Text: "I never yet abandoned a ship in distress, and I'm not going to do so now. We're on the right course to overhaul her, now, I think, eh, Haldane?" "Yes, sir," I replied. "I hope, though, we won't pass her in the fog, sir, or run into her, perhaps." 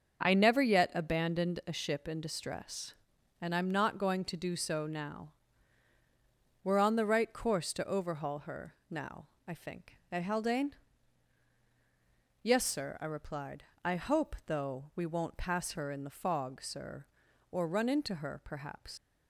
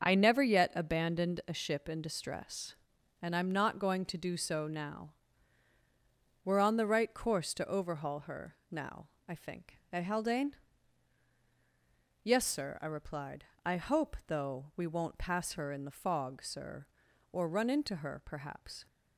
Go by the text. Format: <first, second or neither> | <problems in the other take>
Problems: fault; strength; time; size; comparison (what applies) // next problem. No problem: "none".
second | starts louder than the rest; until 1.2 s; 6.5 dB; also in the second // leaves "perhaps" unfinished; at 18.9 s; 75 ms